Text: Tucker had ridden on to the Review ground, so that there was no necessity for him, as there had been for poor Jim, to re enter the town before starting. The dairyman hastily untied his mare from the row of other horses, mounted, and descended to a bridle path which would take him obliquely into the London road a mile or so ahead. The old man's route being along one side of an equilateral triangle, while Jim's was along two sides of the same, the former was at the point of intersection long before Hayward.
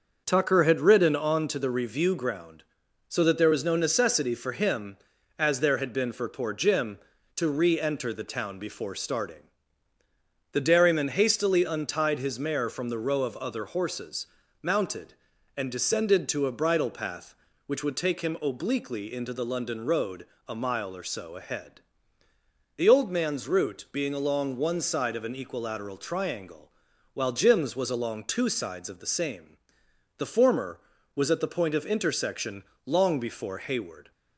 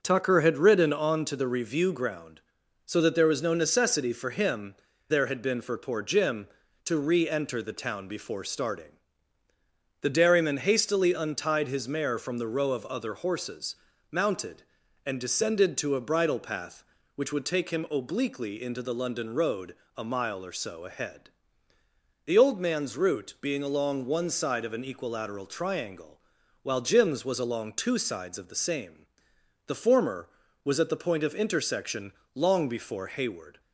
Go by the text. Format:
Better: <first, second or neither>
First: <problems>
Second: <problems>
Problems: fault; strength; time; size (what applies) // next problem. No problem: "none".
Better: first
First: starts louder than the rest; until 1.2 s; 6.5 dB // pauses between "road" and "a"; slight; at 20.2 s; 0.22 s long // pauses between "intersection" and "long"; slight; at 32.6 s; 0.22 s long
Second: starts louder than the rest; noticeable; until 1.0 s; 6 dB // skips "as"; at 4.9 s // pauses between "road" and "a"; slight; at 19.7 s; 0.22 s long // pauses between "intersection" and "long"; slight; at 32.1 s; 0.22 s long